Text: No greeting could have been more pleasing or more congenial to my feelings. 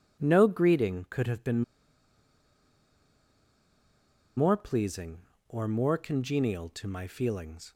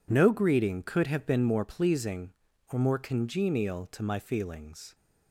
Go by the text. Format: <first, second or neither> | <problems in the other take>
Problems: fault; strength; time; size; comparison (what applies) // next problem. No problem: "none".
second | pauses between "been" and "more"; strong; at 1.6 s; 2.7 s long